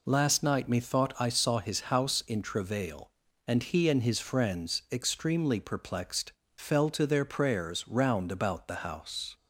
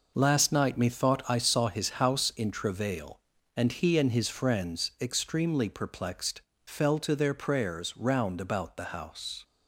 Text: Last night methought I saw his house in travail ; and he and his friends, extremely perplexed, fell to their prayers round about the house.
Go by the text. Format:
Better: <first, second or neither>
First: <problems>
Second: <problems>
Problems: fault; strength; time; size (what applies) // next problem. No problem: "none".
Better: first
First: none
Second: gets quieter; strong; throughout; 8 dB